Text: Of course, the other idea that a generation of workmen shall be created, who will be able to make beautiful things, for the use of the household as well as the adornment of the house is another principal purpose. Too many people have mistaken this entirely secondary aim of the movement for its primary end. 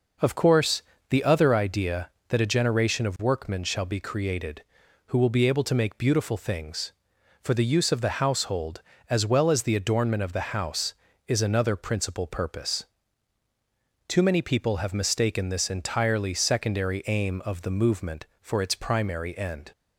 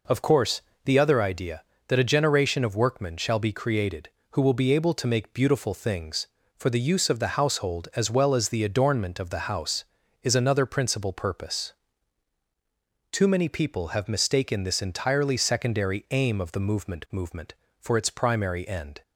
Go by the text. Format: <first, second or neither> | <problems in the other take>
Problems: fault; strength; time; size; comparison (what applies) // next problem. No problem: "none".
first | says "movement" twice; at 17.1 s